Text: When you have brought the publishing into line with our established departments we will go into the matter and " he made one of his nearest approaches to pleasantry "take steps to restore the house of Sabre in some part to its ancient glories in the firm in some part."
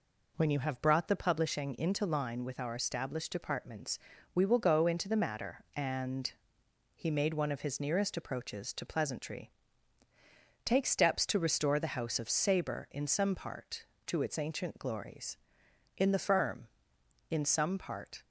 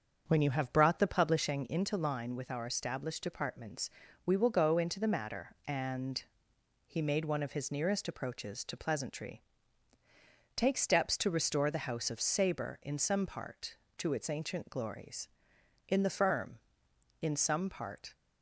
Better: first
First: pauses between "departments" and "we"; slight; at 3.9 s; 0.36 s long // pauses between "pleasantry" and "take"; at 9.4 s; 1.1 s long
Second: starts louder than the rest; until 1.7 s; 7 dB // pauses between "departments" and "we"; slight; at 3.8 s; 0.36 s long // pauses between "pleasantry" and "take"; at 9.4 s; 1.1 s long

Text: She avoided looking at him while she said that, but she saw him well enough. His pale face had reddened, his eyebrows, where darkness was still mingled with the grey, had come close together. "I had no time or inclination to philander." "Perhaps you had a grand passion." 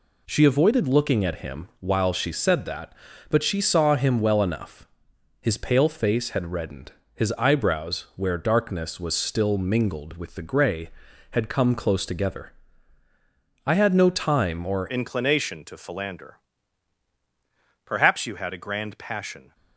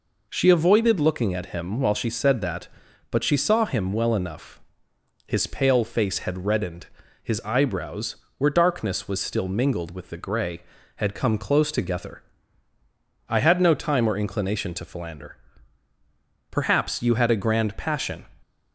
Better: second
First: changes voice at "inclination"; from 14.8 s on; 4.7 s long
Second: none

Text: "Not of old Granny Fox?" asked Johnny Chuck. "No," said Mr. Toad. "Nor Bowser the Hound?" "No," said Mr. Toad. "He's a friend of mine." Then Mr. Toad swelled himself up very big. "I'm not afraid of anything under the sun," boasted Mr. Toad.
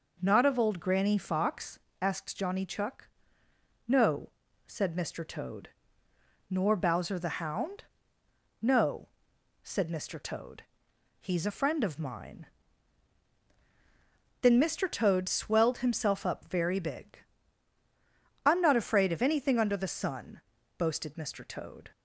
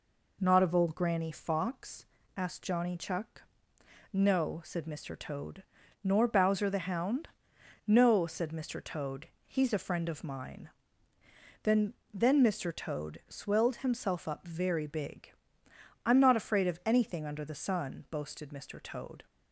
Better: first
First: none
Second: says "Then" twice; at 12.1 s

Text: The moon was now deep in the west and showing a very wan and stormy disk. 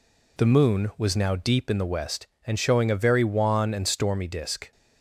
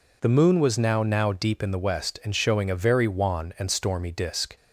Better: first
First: none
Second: says "now" twice; at 1.0 s

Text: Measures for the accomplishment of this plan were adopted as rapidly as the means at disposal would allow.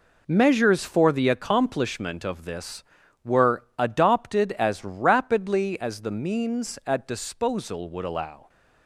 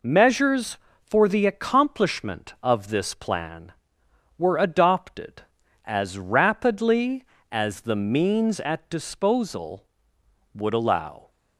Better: second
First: skips "plan"; at 3.0 s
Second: none

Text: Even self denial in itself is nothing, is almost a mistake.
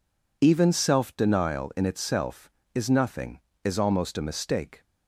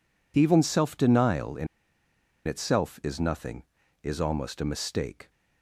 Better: first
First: none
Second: pauses between "in" and "itself"; noticeable; at 1.6 s; 0.80 s long

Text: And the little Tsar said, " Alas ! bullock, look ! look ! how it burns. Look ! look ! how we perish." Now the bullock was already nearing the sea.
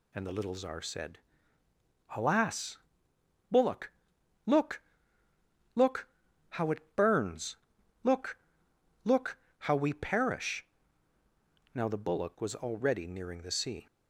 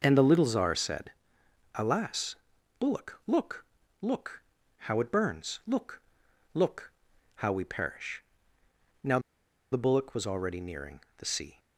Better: first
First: none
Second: pauses between "Now" and "the"; noticeable; at 9.1 s; 0.53 s long // pauses between "nearing" and "the"; slight; at 10.9 s; 0.18 s long

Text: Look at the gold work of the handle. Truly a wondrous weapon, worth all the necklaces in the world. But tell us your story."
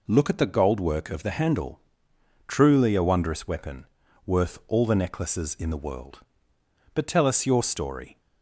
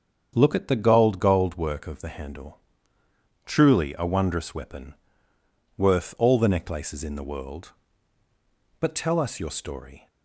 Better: first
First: none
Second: starts louder than the rest; strong; until 1.3 s; 7.5 dB // says "gold" twice; at 1.1 s

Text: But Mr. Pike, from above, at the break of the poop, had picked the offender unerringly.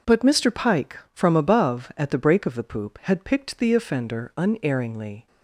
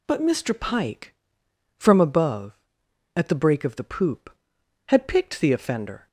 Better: first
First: none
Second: stops before "unerringly"; at 6.0 s

